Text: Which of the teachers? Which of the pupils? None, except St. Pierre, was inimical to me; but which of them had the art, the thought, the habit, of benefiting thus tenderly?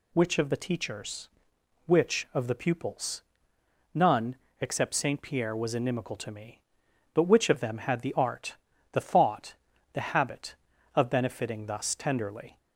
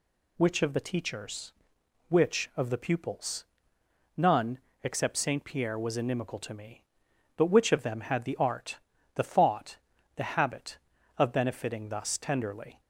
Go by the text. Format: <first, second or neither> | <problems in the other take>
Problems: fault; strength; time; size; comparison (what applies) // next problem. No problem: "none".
neither | none